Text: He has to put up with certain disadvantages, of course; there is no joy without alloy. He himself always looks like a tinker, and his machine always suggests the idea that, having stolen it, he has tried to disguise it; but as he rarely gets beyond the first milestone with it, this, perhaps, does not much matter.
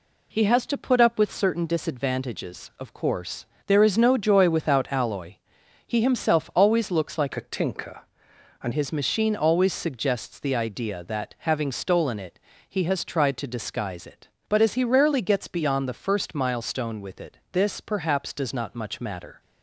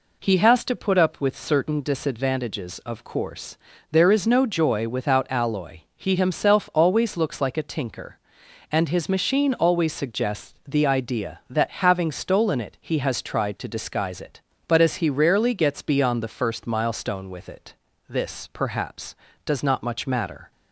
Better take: second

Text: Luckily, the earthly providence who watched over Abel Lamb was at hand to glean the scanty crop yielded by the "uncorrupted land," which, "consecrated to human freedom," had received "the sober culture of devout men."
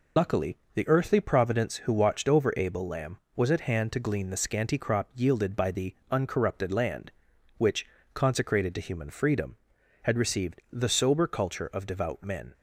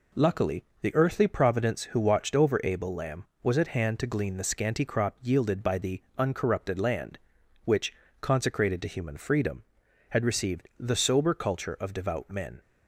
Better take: second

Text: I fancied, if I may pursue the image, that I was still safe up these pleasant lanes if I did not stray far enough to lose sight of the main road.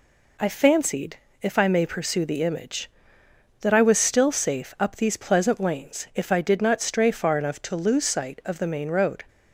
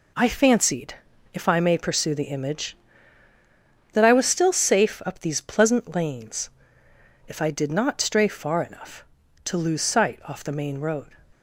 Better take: first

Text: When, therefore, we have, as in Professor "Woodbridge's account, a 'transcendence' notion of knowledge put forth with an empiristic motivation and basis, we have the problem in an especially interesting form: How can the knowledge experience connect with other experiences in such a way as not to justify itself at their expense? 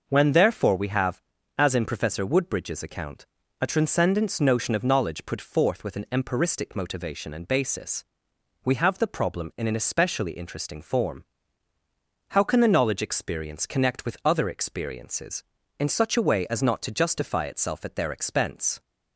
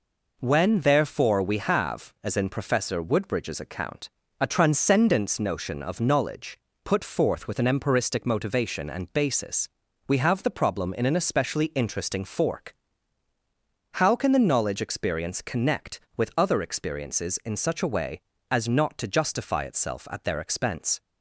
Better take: first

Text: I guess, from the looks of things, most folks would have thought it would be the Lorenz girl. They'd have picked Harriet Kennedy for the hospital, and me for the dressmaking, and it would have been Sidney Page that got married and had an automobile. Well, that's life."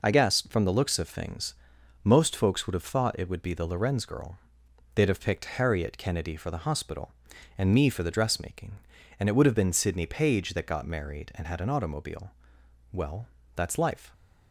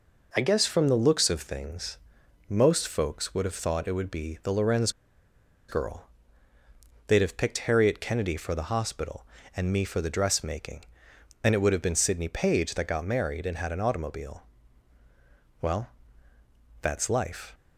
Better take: first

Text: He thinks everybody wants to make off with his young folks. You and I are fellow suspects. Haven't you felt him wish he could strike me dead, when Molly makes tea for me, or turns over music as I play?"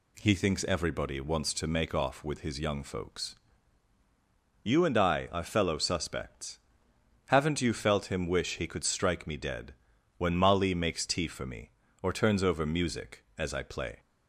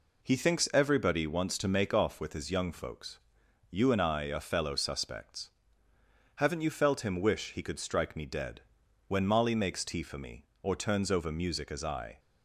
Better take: first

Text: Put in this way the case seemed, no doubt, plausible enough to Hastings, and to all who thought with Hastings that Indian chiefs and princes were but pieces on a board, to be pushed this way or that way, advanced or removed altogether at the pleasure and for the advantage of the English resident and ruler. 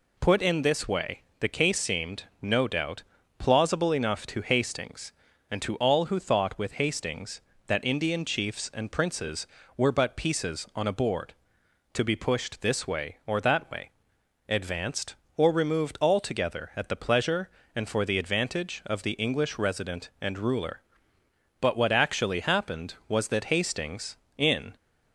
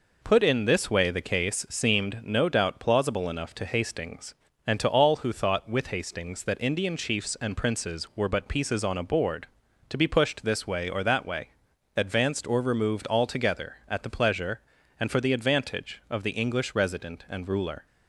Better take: second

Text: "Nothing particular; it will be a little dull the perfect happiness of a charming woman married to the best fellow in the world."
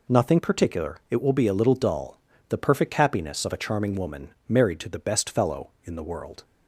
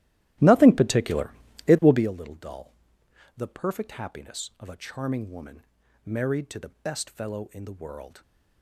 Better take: first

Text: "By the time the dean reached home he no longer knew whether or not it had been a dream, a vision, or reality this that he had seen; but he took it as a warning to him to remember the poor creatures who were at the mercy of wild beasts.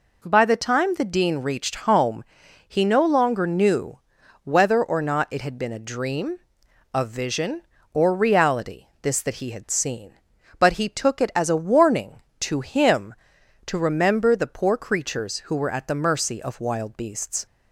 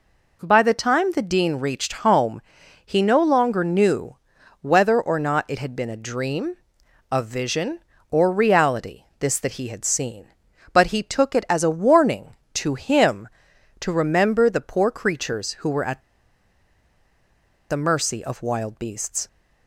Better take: first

